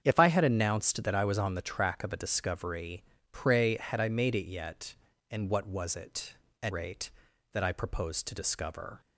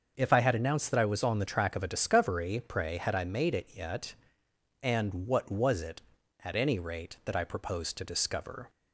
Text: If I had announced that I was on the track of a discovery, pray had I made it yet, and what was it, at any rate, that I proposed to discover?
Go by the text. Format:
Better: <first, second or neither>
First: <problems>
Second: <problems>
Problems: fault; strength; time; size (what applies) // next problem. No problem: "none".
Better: second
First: starts louder than the rest; strong; until 1.0 s; 8 dB // skips "any"; at 6.7 s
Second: starts louder than the rest; until 1.1 s; 6.5 dB